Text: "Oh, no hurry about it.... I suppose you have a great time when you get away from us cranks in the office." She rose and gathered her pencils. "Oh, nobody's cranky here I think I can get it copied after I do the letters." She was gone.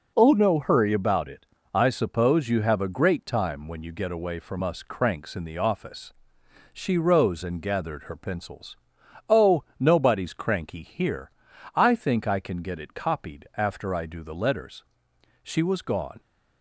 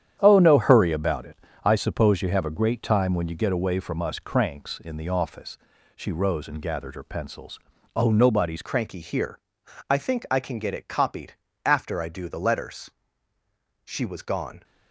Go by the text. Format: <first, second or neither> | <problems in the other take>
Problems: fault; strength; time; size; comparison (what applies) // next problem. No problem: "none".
first | starts louder than the rest; strong; until 1.2 s; 9.5 dB // changes voice at "cranky"; from 8.6 s on; 6.0 s long // pauses between "here" and "I"; noticeable; at 9.4 s; 0.48 s long; also in the first // pauses between "copied" and "after"; slight; at 11.3 s; 0.32 s long